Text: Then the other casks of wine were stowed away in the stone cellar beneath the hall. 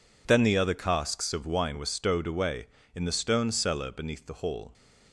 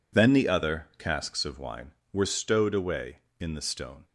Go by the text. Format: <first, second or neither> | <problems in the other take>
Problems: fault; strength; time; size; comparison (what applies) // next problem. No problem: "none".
first | stops before "cellar beneath the hall"; at 4.0 s